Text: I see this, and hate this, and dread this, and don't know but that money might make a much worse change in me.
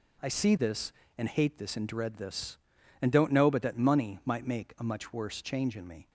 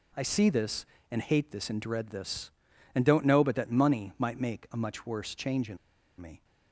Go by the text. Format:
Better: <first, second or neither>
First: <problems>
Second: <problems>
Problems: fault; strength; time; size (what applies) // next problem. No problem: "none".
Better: first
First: none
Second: pauses between "in" and "me"; at 5.7 s; 0.44 s long